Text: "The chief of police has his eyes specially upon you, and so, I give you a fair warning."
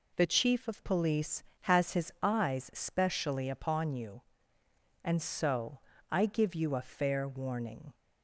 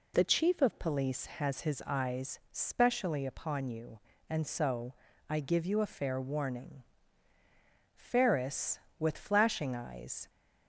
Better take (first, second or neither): first